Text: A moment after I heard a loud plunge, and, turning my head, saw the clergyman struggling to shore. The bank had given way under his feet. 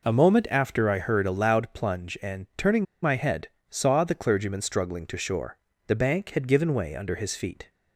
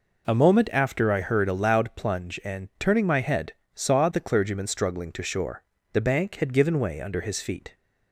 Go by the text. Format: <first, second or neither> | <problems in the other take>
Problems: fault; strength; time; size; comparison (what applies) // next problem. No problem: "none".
second | pauses between "turning" and "my"; slight; at 2.8 s; 0.19 s long